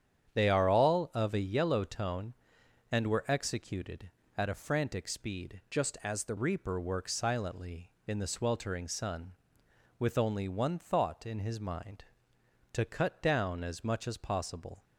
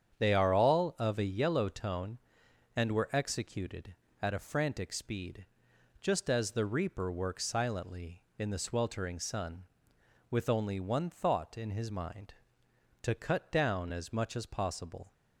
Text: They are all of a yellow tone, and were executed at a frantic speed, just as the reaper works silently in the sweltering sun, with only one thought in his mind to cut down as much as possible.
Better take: second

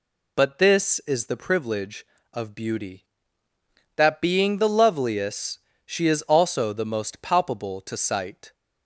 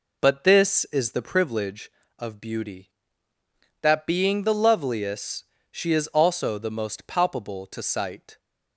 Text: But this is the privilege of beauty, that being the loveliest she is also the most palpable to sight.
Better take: first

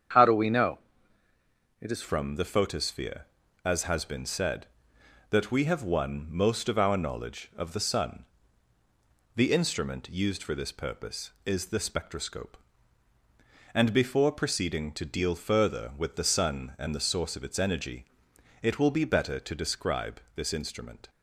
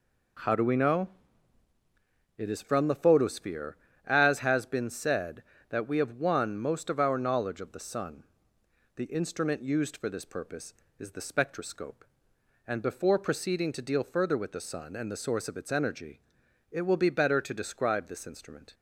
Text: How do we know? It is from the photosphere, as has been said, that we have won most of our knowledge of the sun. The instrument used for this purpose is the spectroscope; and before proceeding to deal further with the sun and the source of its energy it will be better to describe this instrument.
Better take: second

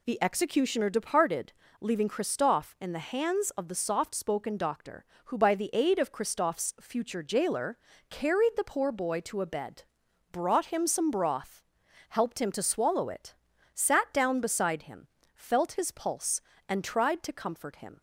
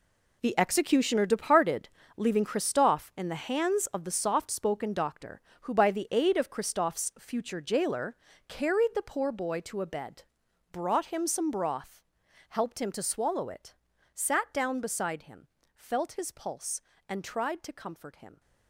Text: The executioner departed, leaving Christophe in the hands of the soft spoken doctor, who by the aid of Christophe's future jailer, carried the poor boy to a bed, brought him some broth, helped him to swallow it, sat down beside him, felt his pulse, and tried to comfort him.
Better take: first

